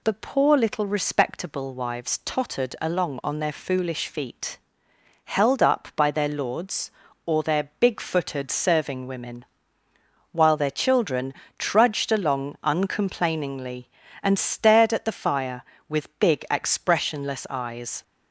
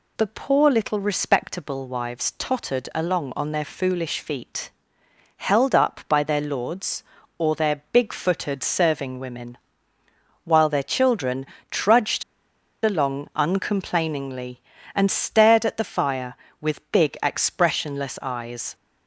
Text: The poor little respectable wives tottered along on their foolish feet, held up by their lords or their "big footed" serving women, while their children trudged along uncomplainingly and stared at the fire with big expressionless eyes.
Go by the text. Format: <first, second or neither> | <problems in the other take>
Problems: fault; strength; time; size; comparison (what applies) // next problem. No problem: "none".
first | pauses between "children" and "trudged"; slight; at 11.4 s; 0.24 s long; slight in the first // pauses between "trudged" and "along"; noticeable; at 12.2 s; 0.61 s long